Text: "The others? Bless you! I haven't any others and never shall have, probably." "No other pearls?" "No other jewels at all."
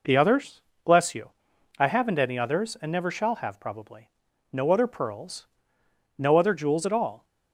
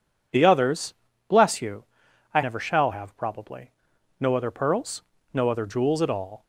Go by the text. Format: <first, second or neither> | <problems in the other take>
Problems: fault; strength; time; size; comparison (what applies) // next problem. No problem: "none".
first | skips "haven't any others and"; at 2.4 s